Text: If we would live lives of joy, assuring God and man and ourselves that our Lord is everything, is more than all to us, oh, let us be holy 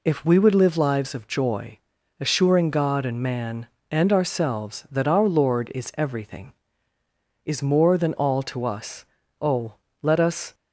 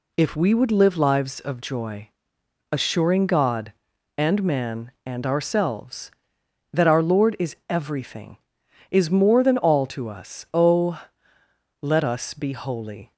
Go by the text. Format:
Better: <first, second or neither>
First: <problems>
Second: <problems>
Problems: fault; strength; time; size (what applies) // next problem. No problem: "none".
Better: second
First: stops before "be holy"; at 10.5 s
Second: none